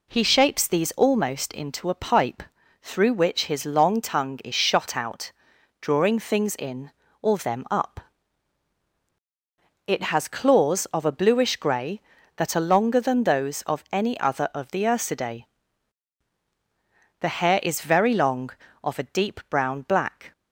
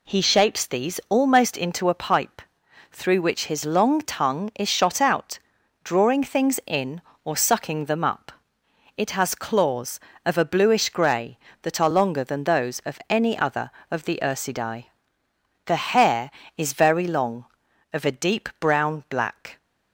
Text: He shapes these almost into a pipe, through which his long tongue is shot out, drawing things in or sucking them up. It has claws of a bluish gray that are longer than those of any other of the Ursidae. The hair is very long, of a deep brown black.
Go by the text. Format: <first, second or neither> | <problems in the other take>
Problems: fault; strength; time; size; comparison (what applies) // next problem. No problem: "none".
second | skips "sucking"; at 7.3 s